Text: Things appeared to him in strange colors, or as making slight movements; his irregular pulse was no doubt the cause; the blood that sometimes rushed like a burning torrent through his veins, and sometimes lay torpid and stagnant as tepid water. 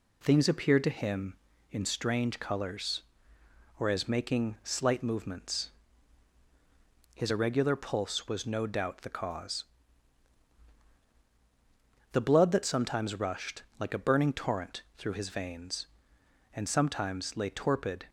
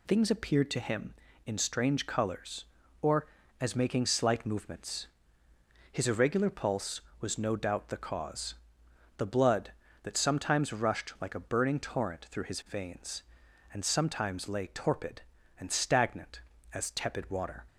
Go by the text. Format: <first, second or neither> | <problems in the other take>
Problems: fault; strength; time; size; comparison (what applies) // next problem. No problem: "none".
second | pauses between "rushed" and "like"; slight; at 13.6 s; 0.16 s long // pauses between "torrent" and "through"; slight; at 14.8 s; 0.16 s long // stops before "and stagnant as tepid water"; at 18.0 s